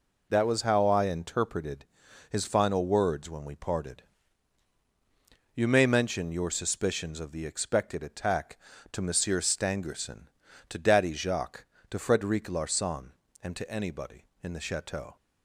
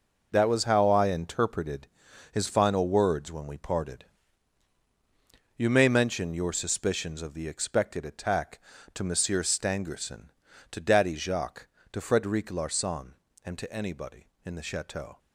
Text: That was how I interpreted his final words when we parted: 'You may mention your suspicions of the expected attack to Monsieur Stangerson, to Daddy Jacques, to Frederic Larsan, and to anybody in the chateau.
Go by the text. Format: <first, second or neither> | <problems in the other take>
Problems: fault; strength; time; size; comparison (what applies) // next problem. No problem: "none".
first | gets quieter; strong; throughout; 9 dB // pauses between "interpreted" and "his"; at 1.8 s; 0.44 s long; also in the first